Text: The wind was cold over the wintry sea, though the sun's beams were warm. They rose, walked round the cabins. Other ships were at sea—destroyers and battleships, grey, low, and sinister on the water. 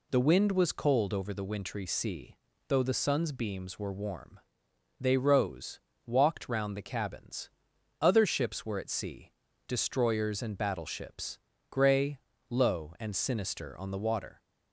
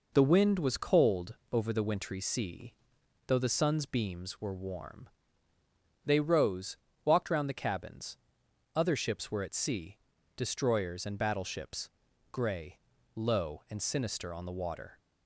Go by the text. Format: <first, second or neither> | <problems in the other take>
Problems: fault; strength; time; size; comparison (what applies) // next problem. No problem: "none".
neither | none